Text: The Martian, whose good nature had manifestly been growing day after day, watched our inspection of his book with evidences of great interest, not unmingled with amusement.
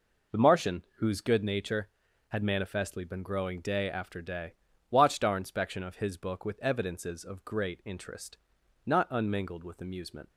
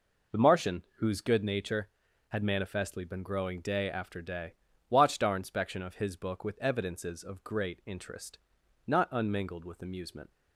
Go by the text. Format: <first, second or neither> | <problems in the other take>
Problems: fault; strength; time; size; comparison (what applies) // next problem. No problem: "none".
neither | none